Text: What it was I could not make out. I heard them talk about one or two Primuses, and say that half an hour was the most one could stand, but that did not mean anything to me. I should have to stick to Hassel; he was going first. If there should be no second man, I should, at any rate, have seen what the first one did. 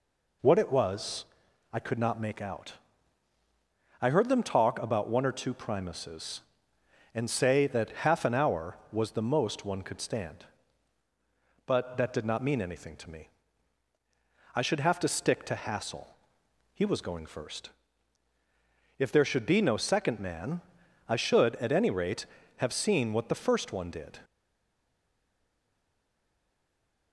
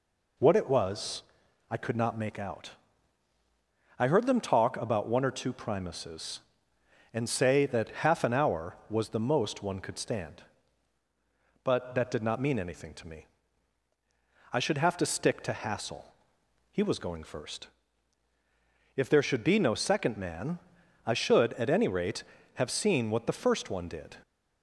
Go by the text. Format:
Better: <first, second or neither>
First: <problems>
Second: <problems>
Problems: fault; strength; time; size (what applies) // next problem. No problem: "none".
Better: second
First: pauses between "was" and "I"; noticeable; at 1.2 s; 0.46 s long // stays silent after the last word; strong; from 24.2 s on; 2.9 s long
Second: pauses between "was" and "I"; noticeable; at 1.2 s; 0.46 s long